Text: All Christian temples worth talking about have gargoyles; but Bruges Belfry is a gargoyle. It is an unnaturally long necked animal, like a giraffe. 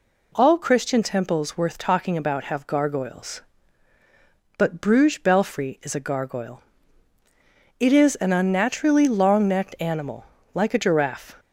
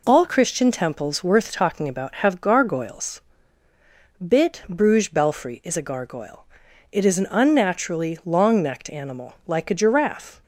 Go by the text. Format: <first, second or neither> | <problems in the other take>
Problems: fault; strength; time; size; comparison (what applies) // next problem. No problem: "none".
first | says "bit" for "but"; at 4.2 s